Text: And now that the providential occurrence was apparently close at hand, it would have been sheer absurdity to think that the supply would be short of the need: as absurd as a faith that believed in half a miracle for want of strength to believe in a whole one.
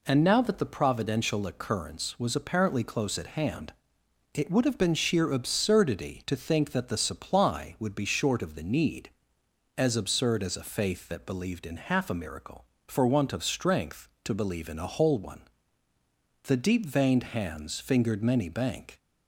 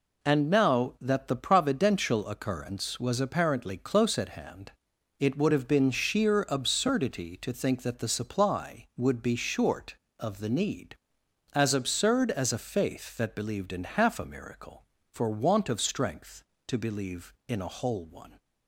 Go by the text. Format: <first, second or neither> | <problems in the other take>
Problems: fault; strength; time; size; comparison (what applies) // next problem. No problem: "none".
second | goes on to say "The deep veined hands fingered many bank"; strong; from 16.4 s on; 2.5 s long